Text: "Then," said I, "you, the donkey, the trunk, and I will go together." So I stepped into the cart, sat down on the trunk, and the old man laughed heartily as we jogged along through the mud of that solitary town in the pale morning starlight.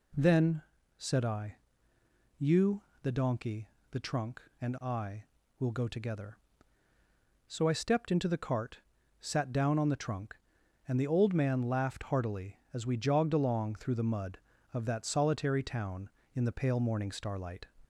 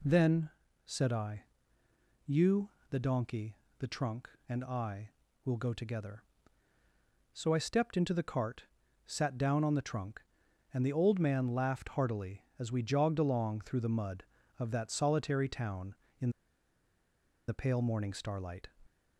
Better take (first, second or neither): first